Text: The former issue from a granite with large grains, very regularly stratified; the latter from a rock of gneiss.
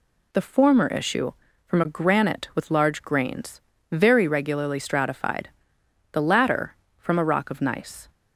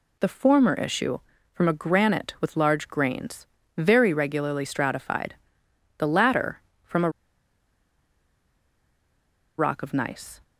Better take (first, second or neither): first